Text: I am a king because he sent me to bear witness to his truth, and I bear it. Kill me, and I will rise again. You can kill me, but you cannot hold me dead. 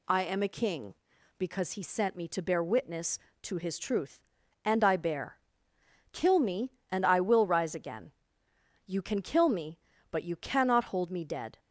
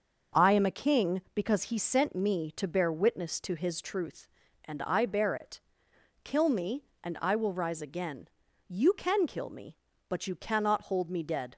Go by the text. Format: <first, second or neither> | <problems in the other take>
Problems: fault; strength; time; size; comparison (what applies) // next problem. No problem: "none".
second | skips "it"; at 5.7 s